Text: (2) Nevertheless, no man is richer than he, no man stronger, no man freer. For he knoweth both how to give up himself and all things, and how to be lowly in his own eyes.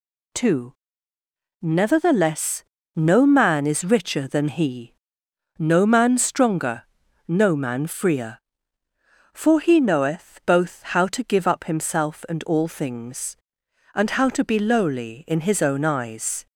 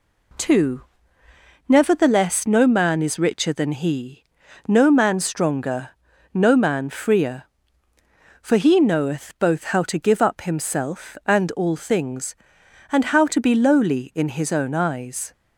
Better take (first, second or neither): neither